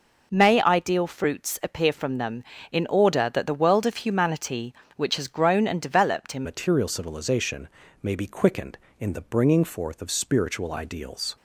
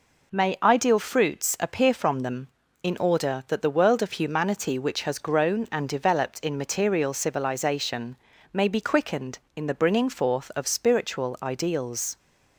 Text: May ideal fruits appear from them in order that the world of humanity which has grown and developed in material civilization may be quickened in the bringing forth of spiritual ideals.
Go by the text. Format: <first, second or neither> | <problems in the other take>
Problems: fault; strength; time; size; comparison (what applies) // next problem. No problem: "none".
second | changes voice at "material"; from 6.4 s on; 4.9 s long // pauses between "civilization" and "may"; slight; at 7.6 s; 0.34 s long; also in the second